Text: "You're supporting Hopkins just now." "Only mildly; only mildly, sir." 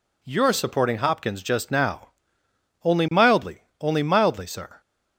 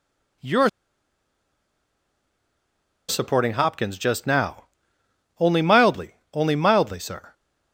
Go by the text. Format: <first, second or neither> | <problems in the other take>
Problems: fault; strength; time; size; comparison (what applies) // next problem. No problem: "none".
first | pauses between "You're" and "supporting"; strong; at 0.6 s; 2.4 s long